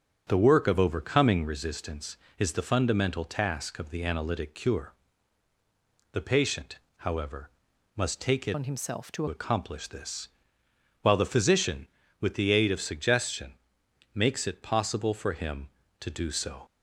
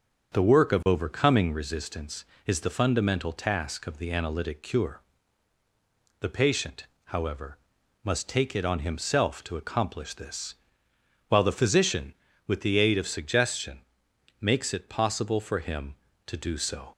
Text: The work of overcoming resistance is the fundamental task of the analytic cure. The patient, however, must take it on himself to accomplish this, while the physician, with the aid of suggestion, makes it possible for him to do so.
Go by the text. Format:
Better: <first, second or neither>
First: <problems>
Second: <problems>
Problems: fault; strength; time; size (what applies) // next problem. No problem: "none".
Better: second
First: starts louder than the rest; until 1.2 s; 7 dB // changes voice from "on" to "to"; from 8.5 to 9.2 s; 0.7 s long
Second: starts louder than the rest; until 1.3 s; 7 dB